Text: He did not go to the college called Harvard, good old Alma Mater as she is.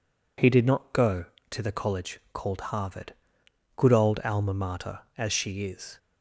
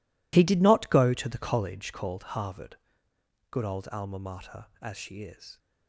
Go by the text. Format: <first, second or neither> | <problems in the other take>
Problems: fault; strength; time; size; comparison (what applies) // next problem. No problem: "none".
first | gets quieter; strong; throughout; 15 dB